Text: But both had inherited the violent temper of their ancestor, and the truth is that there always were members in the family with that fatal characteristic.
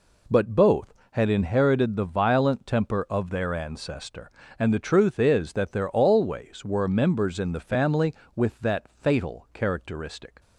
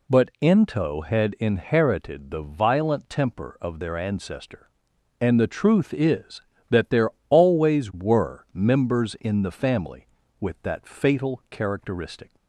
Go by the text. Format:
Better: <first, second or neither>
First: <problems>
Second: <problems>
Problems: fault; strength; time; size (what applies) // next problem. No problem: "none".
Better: first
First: none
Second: says "ento" for "both"; at 0.4 s // pauses between "there" and "always"; slight; at 7.0 s; 0.20 s long